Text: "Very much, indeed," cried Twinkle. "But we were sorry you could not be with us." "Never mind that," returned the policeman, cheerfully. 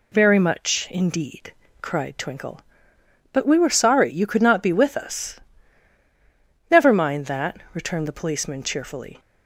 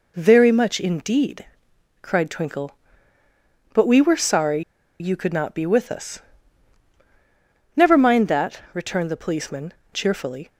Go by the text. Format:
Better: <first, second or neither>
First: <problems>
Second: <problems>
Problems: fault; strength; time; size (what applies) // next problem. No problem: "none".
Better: first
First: none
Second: pauses between "sorry" and "you"; at 4.6 s; 0.39 s long